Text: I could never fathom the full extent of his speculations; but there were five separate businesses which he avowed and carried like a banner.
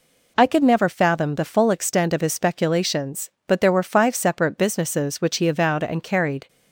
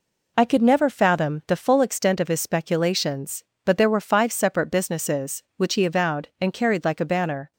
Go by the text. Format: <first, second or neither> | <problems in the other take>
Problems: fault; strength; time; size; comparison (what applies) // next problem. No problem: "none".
second | stops before "like a banner"; at 6.4 s